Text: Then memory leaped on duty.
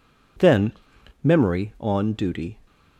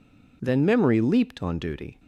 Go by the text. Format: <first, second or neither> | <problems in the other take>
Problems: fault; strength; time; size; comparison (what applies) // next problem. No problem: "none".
second | pauses between "Then" and "memory"; noticeable; at 0.7 s; 0.52 s long // skips "leaped"; at 1.7 s